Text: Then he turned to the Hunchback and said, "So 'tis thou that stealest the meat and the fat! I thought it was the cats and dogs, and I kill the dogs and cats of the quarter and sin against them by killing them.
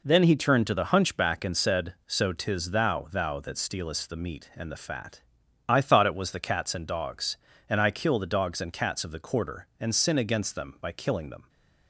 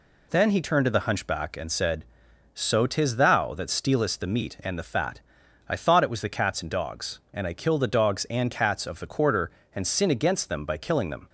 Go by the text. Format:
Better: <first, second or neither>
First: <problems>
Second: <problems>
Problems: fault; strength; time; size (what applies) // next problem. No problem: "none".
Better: second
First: says "thou" twice; at 3.1 s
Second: none